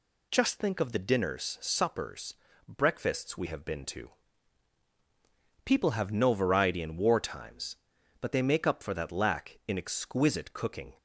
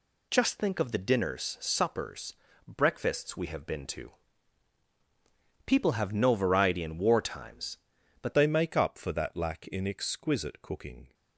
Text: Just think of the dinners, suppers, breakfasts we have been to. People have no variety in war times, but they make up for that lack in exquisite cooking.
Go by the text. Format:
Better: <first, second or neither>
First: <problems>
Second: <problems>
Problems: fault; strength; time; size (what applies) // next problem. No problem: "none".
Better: first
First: none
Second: changes voice at "they"; from 8.3 s on; 2.8 s long